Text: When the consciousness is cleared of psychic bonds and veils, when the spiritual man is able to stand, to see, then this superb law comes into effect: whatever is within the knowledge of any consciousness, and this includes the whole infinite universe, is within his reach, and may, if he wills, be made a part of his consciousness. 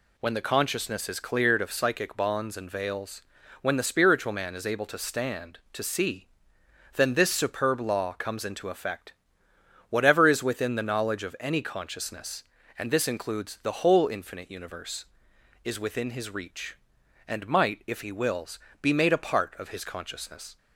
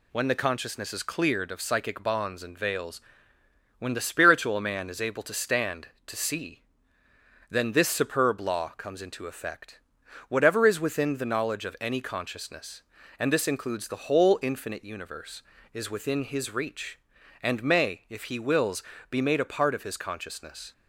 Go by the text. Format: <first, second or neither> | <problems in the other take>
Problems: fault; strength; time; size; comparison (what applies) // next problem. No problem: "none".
second | says "might" for "may"; at 17.4 s